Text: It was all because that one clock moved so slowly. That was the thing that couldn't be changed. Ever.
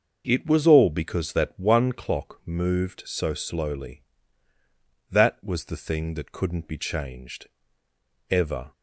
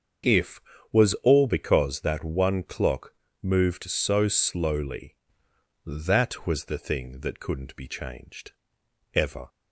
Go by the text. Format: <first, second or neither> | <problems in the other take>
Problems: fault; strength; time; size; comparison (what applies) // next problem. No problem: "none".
first | starts louder than the rest; until 1.6 s; 7 dB; noticeable in the first // says "If" for "It"; at 0.2 s // pauses between "clock" and "moved"; slight; at 3.1 s; 0.30 s long